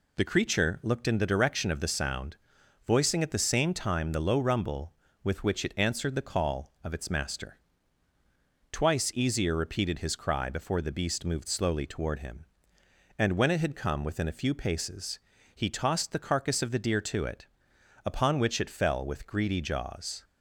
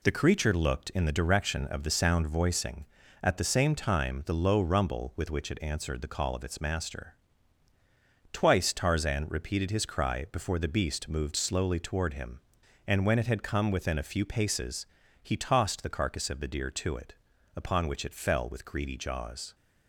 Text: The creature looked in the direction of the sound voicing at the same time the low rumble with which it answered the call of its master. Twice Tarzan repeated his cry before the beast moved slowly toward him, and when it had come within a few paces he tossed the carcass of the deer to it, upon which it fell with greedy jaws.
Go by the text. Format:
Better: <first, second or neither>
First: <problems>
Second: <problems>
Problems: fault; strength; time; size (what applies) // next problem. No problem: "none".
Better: second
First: pauses between "sound" and "voicing"; noticeable; at 2.3 s; 0.52 s long // says "Easier" for "Tarzan"; at 9.1 s // pauses between "paces" and "he"; at 15.1 s; 0.38 s long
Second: pauses between "paces" and "he"; slight; at 14.8 s; 0.36 s long